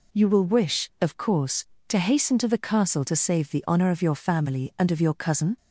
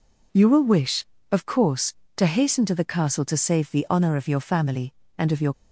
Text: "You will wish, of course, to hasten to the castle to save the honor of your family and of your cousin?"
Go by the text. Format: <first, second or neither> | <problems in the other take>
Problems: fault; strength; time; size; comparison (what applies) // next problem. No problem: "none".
first | stops before "cousin"; at 5.5 s